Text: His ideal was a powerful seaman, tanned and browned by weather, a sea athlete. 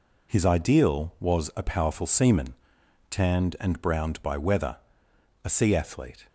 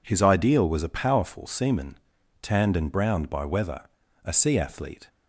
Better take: neither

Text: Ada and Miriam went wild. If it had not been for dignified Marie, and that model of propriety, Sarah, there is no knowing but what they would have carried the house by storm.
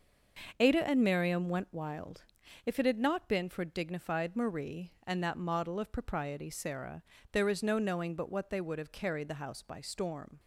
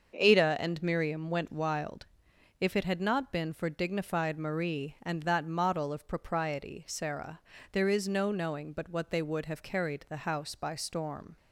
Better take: neither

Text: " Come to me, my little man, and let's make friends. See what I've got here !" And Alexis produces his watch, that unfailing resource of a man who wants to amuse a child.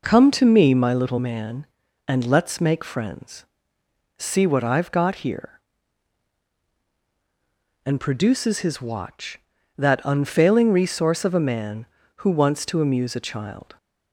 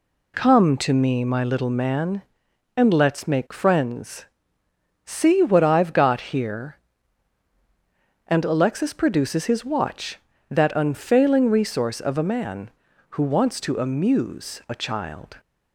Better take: second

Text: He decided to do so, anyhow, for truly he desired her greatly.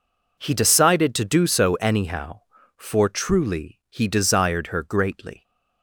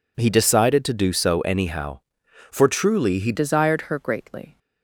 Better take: first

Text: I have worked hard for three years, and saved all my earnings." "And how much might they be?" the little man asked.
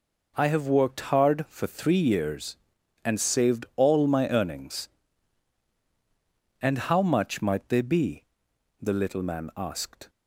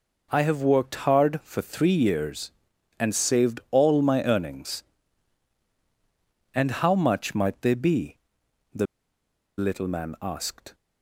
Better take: first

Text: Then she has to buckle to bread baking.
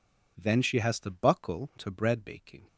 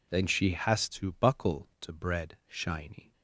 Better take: first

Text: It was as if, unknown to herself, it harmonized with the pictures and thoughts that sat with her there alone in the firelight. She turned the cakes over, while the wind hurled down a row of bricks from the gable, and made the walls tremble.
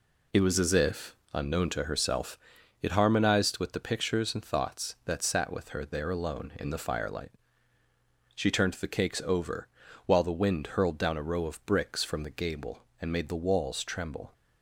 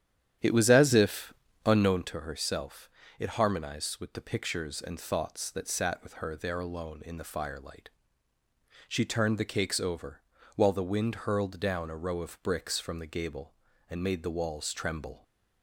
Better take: first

